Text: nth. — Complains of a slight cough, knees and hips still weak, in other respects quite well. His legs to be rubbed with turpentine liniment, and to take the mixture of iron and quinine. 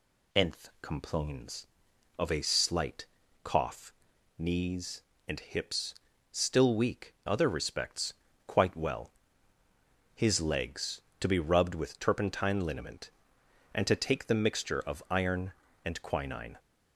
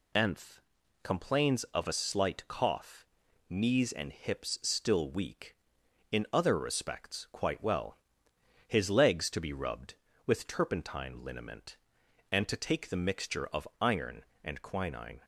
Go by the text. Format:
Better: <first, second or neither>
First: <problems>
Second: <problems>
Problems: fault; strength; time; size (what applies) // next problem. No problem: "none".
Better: second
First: pauses between "slight" and "cough"; at 3.0 s; 0.38 s long // pauses between "hips" and "still"; at 5.9 s; 0.38 s long // skips "in"; at 7.1 s // pauses between "respects" and "quite"; slight; at 8.1 s; 0.32 s long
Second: none